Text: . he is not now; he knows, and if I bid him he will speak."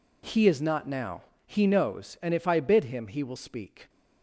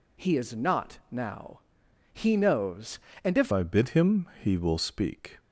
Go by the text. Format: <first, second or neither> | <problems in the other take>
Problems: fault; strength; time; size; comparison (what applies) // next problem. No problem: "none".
first | changes voice at "I"; from 3.5 s on; 1.8 s long